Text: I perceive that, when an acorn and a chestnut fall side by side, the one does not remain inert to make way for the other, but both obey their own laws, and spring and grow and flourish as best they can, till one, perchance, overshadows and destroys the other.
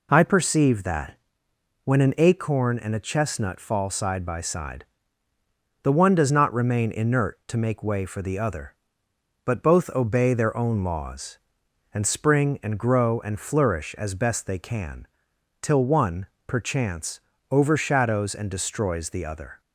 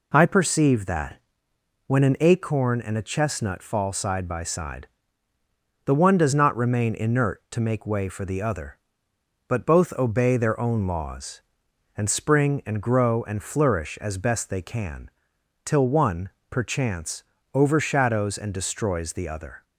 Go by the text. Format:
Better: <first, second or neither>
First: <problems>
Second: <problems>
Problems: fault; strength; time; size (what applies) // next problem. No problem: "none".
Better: neither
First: none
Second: none